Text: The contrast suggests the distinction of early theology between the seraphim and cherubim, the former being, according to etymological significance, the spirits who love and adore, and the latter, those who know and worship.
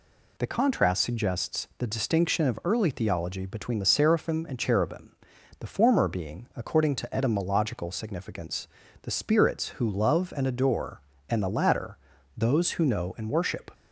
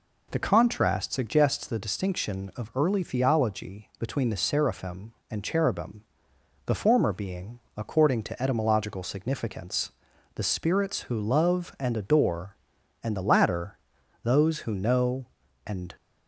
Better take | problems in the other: first | stops before "worship"; at 15.9 s

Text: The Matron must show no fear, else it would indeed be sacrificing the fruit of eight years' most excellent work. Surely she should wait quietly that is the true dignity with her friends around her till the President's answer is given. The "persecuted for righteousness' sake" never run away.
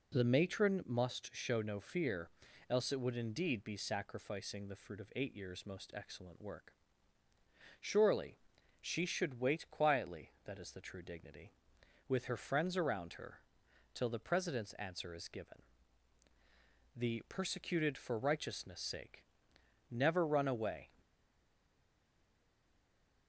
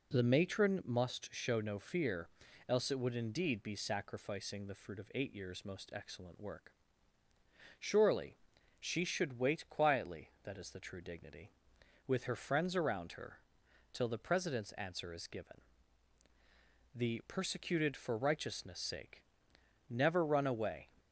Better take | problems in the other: second | pauses between "Surely" and "she"; at 8.3 s; 0.42 s long; also in the second // pauses between "her" and "till"; noticeable; at 13.3 s; 0.56 s long; noticeable in the second // pauses between "sake" and "never"; noticeable; at 19.2 s; 0.66 s long; noticeable in the second // stays silent after the last word; from 20.9 s on; 2.3 s long

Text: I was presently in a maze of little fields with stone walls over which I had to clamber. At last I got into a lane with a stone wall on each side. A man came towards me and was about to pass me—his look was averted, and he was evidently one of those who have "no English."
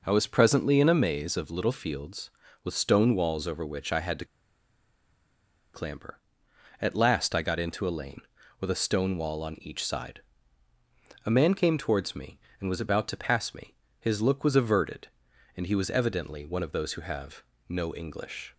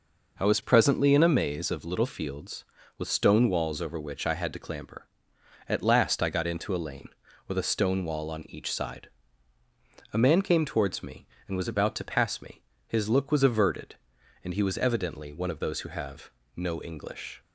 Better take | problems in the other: second | pauses between "to" and "clamber"; strong; at 4.2 s; 1.4 s long // pauses between "have" and "no"; slight; at 17.4 s; 0.26 s long; slight in the second

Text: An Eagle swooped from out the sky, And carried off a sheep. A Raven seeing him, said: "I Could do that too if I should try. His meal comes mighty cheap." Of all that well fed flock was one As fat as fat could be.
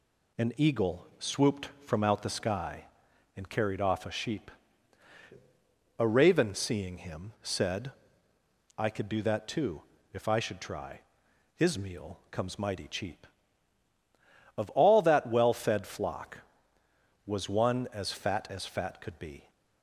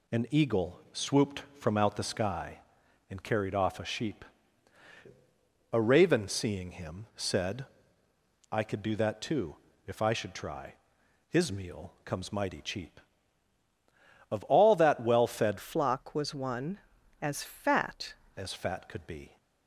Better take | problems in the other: first | pauses between "too" and "if"; slight; at 9.5 s; 0.30 s long; slight in the first // changes voice from "flock" to "fat"; from 15.5 to 18.1 s; 2.6 s long

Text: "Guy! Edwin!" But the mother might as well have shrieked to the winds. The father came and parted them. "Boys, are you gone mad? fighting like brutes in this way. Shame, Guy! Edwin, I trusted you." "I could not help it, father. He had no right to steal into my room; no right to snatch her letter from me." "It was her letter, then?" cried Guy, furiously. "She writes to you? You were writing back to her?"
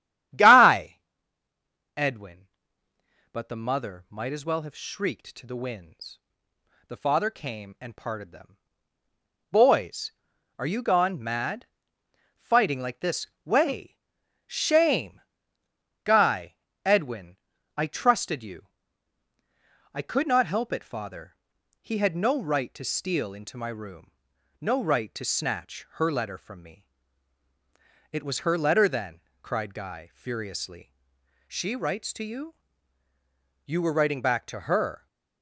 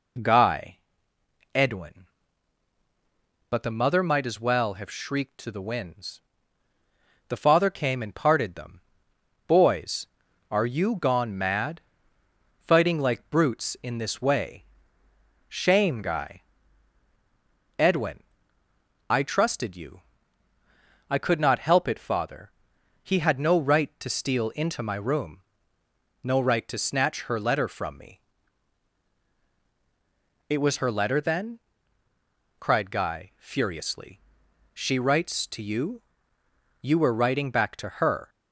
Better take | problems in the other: second | starts louder than the rest; strong; until 2.3 s; 10.5 dB // skips "brutes in"; at 13.0 s // pauses between "this" and "way"; slight; at 13.2 s; 0.18 s long

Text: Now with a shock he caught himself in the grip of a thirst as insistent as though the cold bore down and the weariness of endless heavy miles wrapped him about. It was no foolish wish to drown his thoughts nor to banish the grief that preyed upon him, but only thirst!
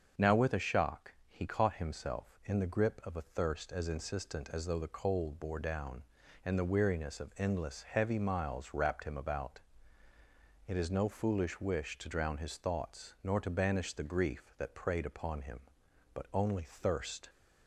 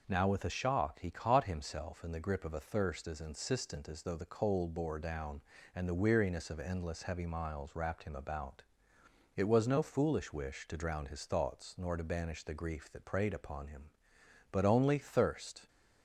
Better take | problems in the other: second | starts louder than the rest; until 1.3 s; 6.5 dB // pauses between "shock" and "he"; slight; at 1.1 s; 0.16 s long // says "is" for "was"; at 10.7 s

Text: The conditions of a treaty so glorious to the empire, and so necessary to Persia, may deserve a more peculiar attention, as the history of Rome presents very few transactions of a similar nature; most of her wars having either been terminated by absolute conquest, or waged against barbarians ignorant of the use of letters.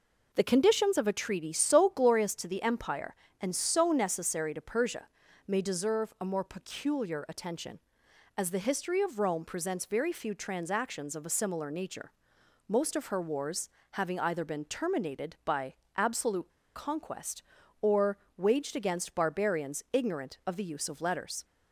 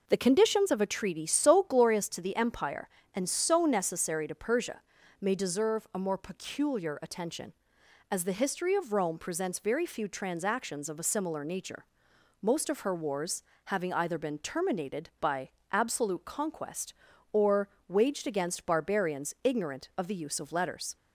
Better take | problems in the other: second | pauses between "wars" and "having"; slight; at 13.6 s; 0.22 s long; slight in the second // pauses between "by" and "absolute"; slight; at 15.7 s; 0.24 s long; slight in the second // pauses between "absolute" and "conquest"; slight; at 16.4 s; 0.27 s long // pauses between "or" and "waged"; slight; at 18.1 s; 0.22 s long; slight in the second

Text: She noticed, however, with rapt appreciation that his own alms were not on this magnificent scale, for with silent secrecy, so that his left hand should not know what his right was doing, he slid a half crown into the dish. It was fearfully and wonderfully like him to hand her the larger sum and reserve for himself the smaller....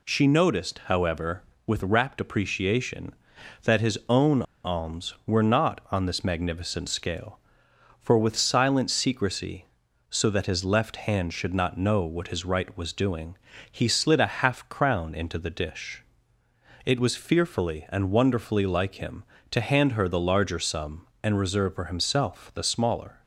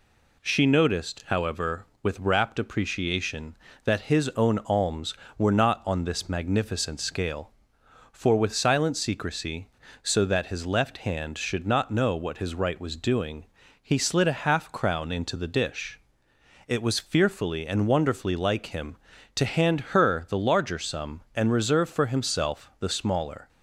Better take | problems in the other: second | pauses between "own" and "alms"; slight; at 4.4 s; 0.21 s long

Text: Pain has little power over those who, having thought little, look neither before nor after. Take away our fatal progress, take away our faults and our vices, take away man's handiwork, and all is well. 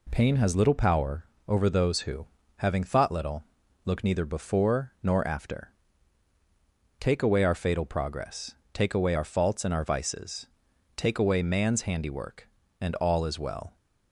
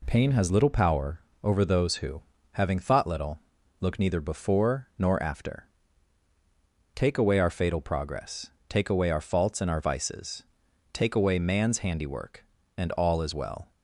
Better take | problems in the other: neither | pauses between "power" and "over"; slight; the same in both

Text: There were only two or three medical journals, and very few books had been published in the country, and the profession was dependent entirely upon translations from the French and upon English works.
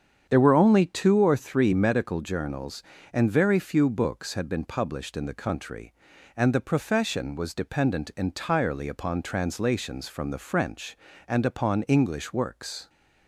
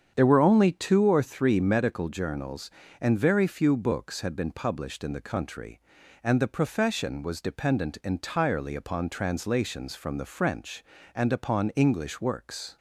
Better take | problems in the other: neither | starts louder than the rest; strong; the same in both

